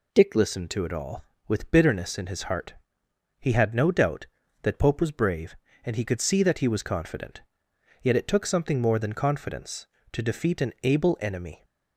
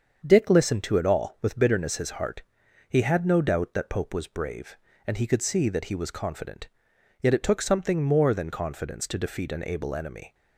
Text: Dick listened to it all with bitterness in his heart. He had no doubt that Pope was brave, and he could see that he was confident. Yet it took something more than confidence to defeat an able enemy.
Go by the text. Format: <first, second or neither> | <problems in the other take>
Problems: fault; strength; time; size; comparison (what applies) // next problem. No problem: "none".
first | starts louder than the rest; until 1.2 s; 7 dB // skips "in"; at 1.9 s